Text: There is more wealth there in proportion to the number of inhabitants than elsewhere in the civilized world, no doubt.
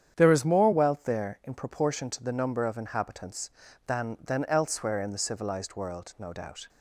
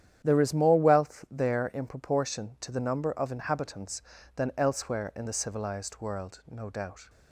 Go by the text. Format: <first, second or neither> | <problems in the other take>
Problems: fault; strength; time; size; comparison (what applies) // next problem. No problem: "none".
second | starts louder than the rest; strong; until 1.1 s; 9 dB; strong in the second // says "than" twice; at 4.2 s